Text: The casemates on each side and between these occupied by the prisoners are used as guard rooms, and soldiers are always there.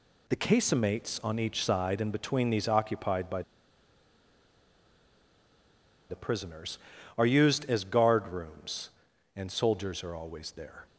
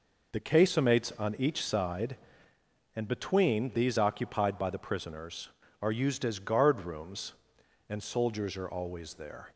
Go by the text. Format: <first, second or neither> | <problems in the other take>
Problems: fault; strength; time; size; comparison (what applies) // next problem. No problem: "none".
second | pauses between "by" and "the"; strong; at 3.4 s; 2.6 s long